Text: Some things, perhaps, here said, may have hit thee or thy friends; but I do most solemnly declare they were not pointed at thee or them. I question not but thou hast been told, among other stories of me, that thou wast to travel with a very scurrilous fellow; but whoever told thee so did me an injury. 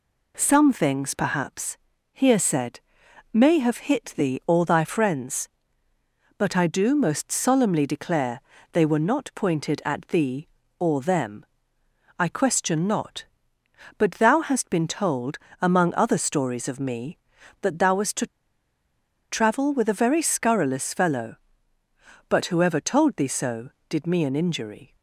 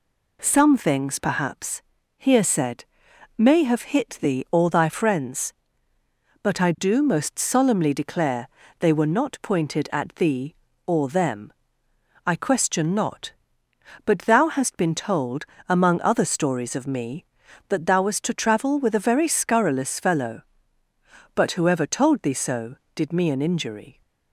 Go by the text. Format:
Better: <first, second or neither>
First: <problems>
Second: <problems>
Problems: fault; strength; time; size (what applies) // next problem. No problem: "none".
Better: second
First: pauses between "declare" and "they"; slight; at 8.4 s; 0.30 s long // pauses between "to" and "travel"; at 18.2 s; 1.0 s long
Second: pauses between "declare" and "they"; slight; at 8.4 s; 0.30 s long